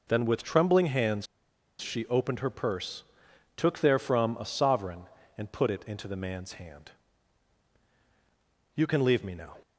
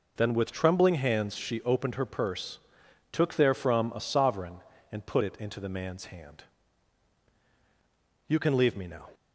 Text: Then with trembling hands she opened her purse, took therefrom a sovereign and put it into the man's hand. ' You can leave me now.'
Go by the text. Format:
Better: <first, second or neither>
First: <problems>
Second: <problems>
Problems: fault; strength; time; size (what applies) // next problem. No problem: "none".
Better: second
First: pauses between "hands" and "she"; noticeable; at 1.2 s; 0.53 s long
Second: none